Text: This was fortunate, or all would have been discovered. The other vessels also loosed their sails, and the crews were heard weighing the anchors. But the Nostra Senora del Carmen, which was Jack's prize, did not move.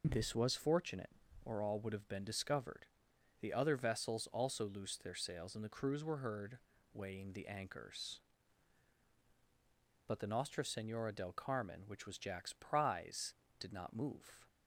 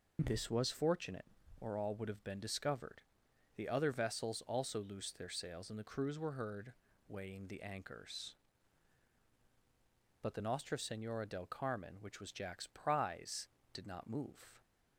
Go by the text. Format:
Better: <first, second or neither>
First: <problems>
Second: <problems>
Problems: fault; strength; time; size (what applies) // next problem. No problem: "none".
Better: neither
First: pauses between "heard" and "weighing"; slight; at 6.5 s; 0.34 s long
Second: pauses between "heard" and "weighing"; slight; at 6.7 s; 0.34 s long